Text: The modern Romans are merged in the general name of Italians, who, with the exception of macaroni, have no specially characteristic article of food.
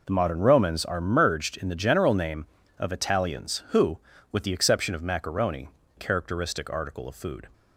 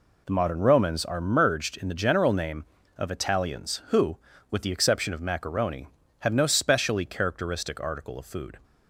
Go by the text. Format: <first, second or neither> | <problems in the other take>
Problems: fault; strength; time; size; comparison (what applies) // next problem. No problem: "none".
second | skips "have no specially"; at 5.8 s